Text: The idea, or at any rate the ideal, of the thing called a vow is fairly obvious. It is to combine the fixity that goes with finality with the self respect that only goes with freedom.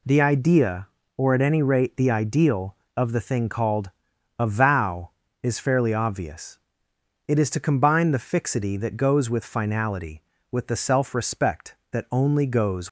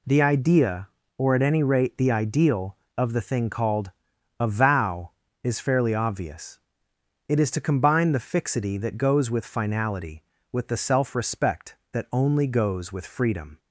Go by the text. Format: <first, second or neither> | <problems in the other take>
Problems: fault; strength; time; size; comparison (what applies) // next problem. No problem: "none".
second | pauses between "called" and "a"; noticeable; at 3.8 s; 0.48 s long; noticeable in the second // stops before "with freedom"; at 12.8 s